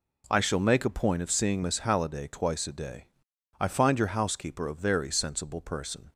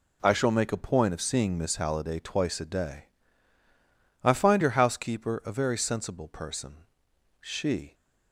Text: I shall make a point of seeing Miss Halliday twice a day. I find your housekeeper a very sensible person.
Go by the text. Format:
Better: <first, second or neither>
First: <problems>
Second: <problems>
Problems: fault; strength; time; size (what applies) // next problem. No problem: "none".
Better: first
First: none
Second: goes on to say "She"; from 7.3 s on; 0.54 s long